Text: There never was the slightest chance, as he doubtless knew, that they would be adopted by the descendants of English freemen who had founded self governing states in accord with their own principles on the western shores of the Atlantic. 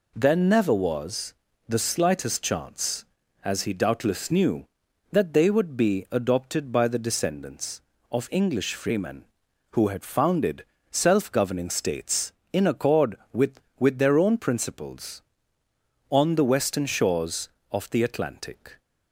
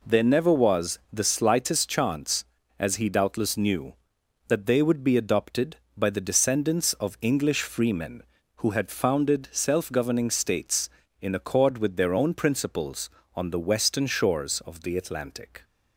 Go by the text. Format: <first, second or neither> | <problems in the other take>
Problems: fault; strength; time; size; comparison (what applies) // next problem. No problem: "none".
second | pauses between "was" and "the"; slight; at 1.3 s; 0.36 s long // pauses between "founded" and "self"; slight; at 10.6 s; 0.24 s long // says "with" twice; at 13.7 s